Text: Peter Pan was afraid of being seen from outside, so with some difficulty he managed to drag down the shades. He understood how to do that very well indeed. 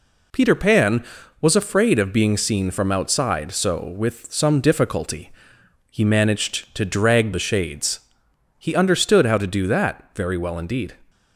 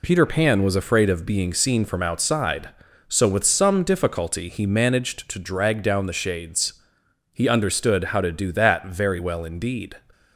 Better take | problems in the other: second | pauses between "difficulty" and "he"; noticeable; at 5.2 s; 0.60 s long // skips "down"; at 7.3 s

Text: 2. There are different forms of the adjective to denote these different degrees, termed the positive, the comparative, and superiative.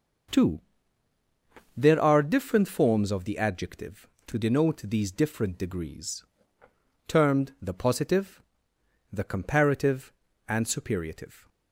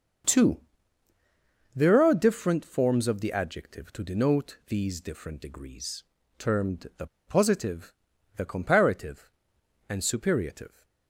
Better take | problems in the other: first | starts louder than the rest; until 2.4 s; 6.5 dB; noticeable in the first // pauses between "the" and "positive"; slight; at 7.0 s; 0.21 s long

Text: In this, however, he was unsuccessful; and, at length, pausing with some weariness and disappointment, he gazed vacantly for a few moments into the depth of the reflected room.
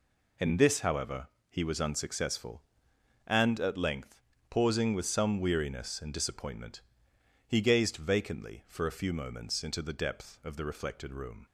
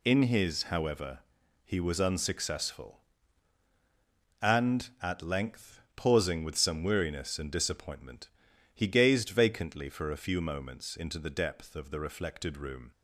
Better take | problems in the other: first | says "his" for "this"; at 0.2 s

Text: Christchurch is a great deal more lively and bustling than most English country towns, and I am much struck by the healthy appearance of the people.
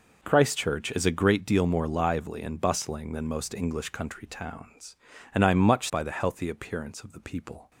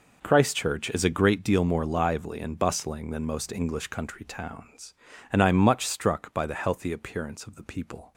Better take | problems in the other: second | skips "struck"; at 5.8 s

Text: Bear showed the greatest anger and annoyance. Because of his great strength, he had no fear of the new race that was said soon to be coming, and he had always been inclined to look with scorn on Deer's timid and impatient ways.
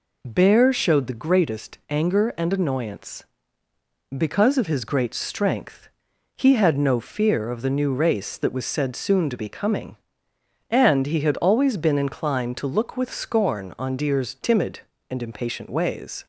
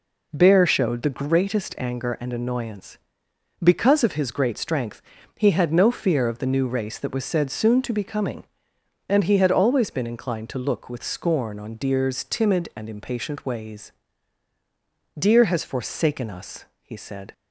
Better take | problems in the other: first | goes on to say "Deer has forsaken us he said"; strong; from 15.1 s on; 2.1 s long

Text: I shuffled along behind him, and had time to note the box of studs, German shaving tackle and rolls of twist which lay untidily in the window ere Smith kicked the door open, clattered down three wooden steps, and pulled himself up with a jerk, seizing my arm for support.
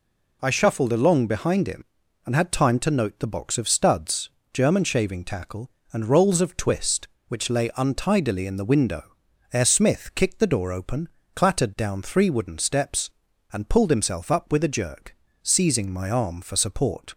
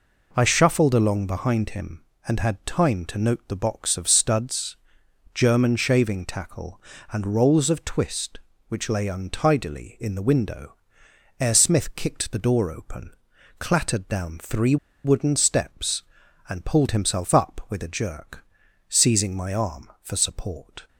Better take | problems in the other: first | pauses between "window" and "ere"; noticeable; at 10.7 s; 0.64 s long; also in the first // pauses between "three" and "wooden"; slight; at 14.7 s; 0.28 s long

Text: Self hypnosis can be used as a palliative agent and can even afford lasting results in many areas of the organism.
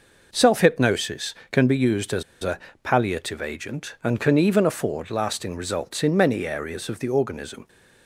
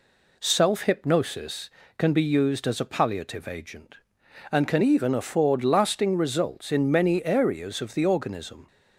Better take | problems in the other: second | pauses between "as" and "a"; slight; at 2.2 s; 0.20 s long // pauses between "a" and "palliative"; slight; at 2.5 s; 0.24 s long

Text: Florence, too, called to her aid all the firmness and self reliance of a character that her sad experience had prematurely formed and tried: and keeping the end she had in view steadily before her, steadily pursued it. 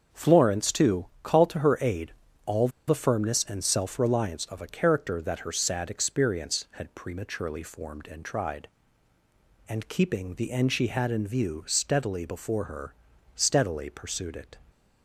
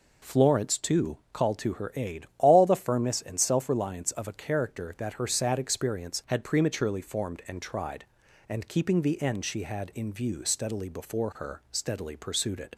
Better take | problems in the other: second | starts louder than the rest; until 1.2 s; 6.5 dB // pauses between "aid" and "all"; slight; at 2.1 s; 0.32 s long // pauses between "all" and "the"; slight; at 2.6 s; 0.19 s long

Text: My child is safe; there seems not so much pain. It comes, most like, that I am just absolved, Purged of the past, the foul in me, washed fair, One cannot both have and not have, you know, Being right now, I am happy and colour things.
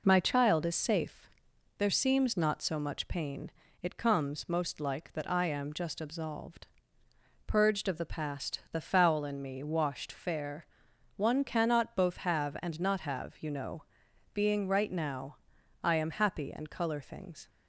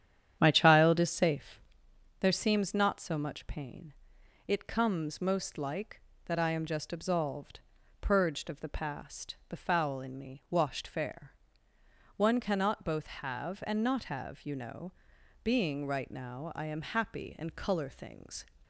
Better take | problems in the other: first | starts louder than the rest; strong; until 1.8 s; 10 dB

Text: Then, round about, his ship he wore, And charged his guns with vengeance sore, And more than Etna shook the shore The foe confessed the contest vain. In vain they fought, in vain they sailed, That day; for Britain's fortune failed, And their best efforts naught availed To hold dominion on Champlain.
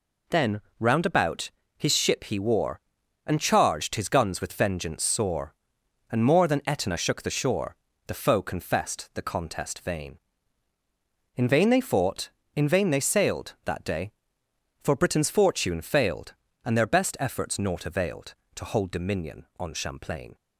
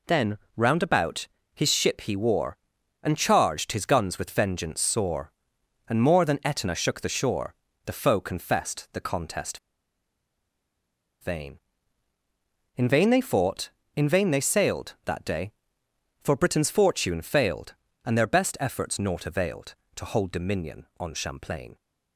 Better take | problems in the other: first | pauses between "shore" and "The"; slight; at 7.5 s; 0.32 s long; slight in the first // pauses between "contest" and "vain"; strong; at 9.5 s; 1.6 s long

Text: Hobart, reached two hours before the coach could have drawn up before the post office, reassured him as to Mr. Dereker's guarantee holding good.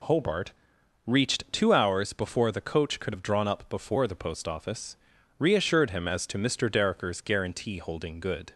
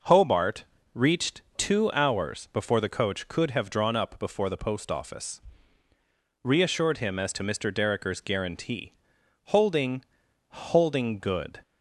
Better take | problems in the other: first | pauses between "guarantee" and "holding"; noticeable; at 8.9 s; 0.50 s long // says "holding" twice; at 10.4 s

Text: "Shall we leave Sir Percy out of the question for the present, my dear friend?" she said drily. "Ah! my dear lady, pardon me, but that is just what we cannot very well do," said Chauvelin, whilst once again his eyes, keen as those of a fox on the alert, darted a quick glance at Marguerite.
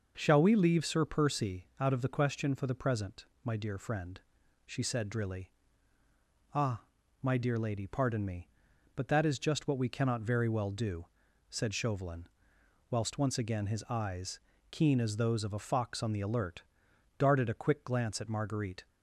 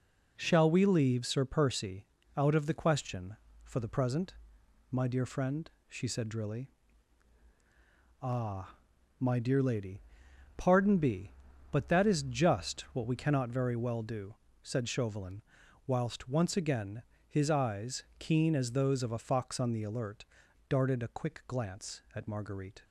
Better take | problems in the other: first | pauses between "Percy" and "out"; slight; at 2.0 s; 0.30 s long // says "be" for "me"; at 10.9 s // pauses between "again" and "his"; slight; at 17.0 s; 0.28 s long

